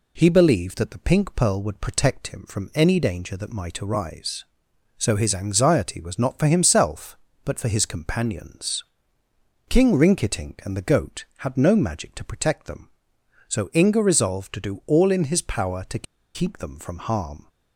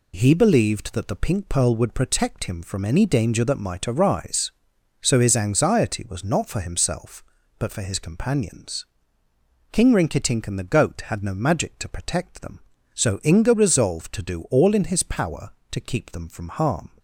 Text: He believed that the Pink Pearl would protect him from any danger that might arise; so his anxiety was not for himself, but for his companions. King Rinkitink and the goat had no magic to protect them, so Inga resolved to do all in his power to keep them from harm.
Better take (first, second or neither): second